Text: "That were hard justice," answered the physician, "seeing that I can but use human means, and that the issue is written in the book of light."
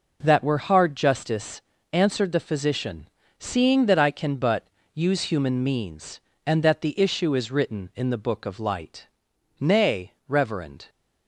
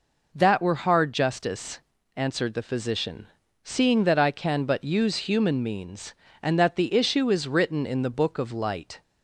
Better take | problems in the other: second | pauses between "but" and "use"; slight; at 4.6 s; 0.26 s long // goes on to say "Nay reverend"; noticeable; from 9.5 s on; 1.3 s long

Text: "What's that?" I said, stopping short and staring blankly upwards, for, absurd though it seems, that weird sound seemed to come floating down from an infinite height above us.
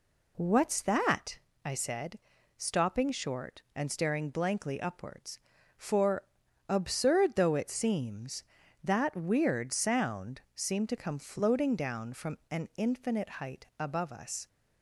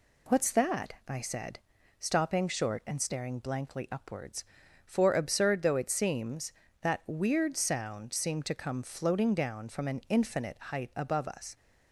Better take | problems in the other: neither | none

